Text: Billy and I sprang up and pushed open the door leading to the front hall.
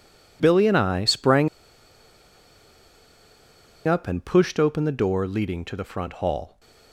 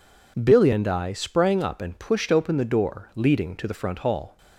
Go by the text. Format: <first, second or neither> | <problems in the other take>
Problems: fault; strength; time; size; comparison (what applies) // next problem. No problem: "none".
second | pauses between "sprang" and "up"; strong; at 1.4 s; 2.3 s long